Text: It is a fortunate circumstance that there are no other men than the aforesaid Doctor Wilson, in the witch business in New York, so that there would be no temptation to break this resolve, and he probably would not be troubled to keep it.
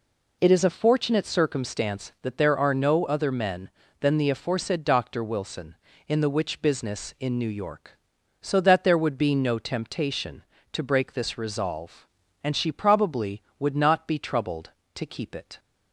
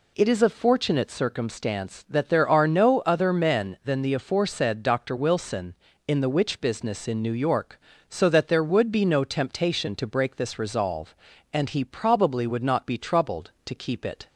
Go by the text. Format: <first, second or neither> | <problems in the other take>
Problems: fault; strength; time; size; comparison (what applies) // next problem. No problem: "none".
second | says "she" for "he"; at 12.5 s